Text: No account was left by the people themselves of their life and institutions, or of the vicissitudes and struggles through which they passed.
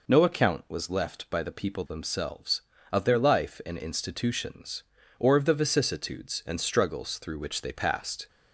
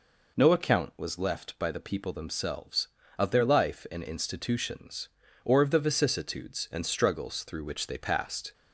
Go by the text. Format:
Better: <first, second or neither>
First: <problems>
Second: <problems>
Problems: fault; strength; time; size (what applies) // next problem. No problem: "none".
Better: neither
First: none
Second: none